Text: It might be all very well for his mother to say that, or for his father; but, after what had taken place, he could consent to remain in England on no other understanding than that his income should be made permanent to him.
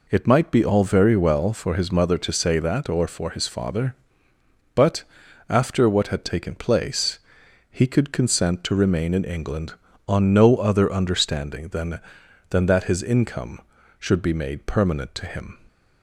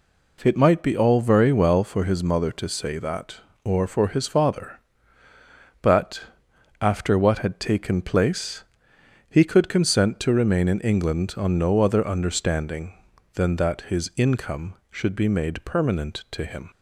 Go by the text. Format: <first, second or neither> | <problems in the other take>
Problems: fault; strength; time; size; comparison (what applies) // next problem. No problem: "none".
second | says "than" twice; at 12.5 s